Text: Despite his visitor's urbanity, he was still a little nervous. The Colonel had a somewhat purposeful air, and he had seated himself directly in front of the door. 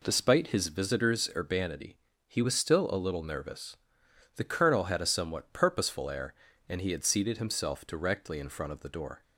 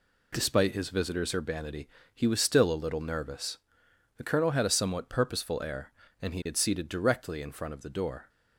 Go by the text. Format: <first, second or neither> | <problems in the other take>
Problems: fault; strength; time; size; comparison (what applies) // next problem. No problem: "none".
first | skips "himself"; at 6.8 s